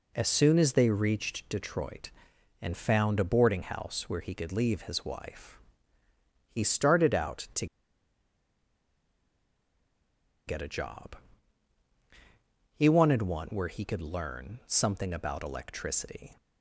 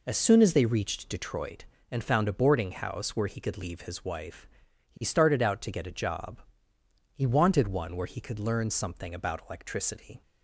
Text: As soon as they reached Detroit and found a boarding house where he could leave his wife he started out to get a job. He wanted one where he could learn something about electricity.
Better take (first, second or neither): second